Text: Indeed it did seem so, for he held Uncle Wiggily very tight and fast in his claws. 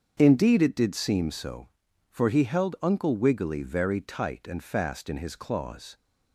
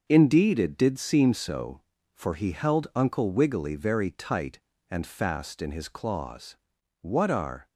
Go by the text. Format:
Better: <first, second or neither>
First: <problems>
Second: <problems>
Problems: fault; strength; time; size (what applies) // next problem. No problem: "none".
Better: first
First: starts louder than the rest; until 1.2 s; 7 dB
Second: starts louder than the rest; until 1.0 s; 6.5 dB // goes on to say "What are"; noticeable; from 7.0 s on; 0.66 s long